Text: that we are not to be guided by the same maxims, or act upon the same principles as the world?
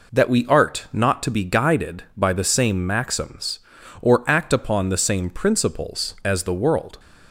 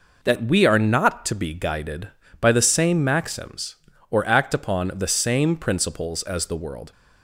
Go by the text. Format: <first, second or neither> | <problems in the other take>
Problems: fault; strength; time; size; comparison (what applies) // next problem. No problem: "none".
second | says "art" for "are"; at 0.4 s